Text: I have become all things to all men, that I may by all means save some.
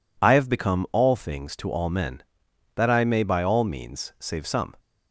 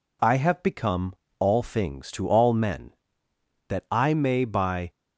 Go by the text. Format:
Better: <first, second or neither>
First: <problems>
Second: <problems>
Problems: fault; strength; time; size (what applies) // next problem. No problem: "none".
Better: first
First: none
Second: pauses between "become" and "all"; slight; at 1.1 s; 0.24 s long // stops before "all means save some"; at 4.9 s